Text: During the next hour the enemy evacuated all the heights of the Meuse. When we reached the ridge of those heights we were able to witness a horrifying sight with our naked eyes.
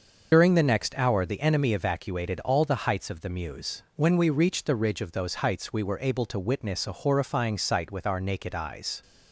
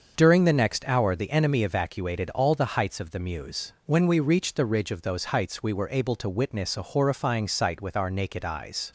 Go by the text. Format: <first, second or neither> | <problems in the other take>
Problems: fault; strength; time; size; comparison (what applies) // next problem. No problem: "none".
second | loses the start of "During"; at 0.3 s; 45 ms // starts louder than the rest; until 1.3 s; 6.5 dB; also in the second